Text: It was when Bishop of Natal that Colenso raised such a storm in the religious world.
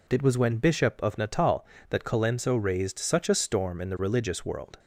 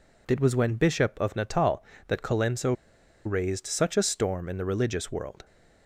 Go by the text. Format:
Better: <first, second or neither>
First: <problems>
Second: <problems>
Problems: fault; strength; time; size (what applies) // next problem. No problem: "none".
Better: first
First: none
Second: pauses between "Colenso" and "raised"; noticeable; at 2.7 s; 0.52 s long